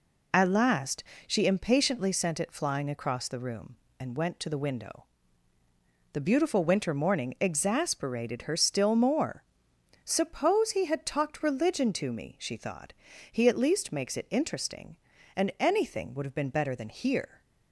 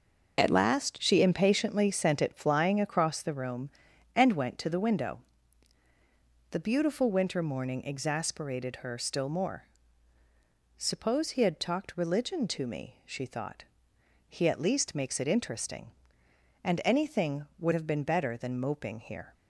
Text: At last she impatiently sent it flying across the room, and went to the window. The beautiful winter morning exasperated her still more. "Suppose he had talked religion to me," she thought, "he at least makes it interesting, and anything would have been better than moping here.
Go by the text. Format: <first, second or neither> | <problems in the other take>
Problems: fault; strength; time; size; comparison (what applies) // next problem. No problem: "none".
second | pauses between "last" and "she"; slight; at 1.0 s; 0.22 s long // skips "moping"; at 16.8 s